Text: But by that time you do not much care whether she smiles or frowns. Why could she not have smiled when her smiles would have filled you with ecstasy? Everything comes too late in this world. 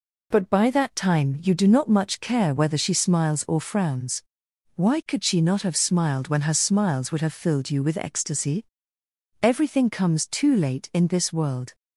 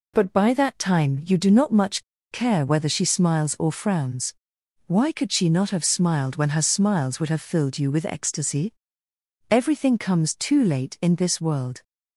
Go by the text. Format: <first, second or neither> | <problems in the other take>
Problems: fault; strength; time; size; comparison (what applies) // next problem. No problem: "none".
first | pauses between "much" and "care"; slight; at 2.0 s; 0.29 s long